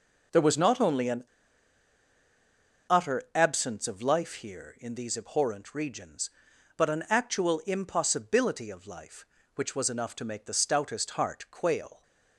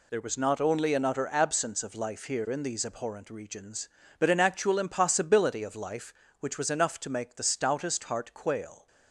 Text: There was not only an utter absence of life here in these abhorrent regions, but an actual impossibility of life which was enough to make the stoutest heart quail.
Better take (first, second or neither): second